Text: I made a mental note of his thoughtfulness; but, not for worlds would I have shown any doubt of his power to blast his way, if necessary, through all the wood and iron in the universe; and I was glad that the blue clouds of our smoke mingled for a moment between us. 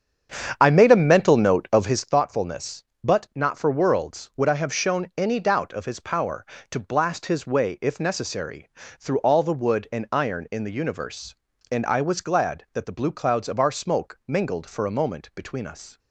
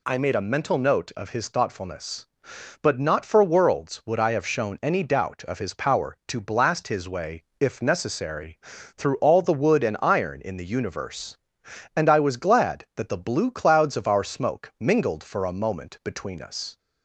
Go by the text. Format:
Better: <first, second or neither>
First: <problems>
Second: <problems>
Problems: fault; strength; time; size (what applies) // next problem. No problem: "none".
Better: second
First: starts louder than the rest; strong; until 2.2 s; 8 dB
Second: none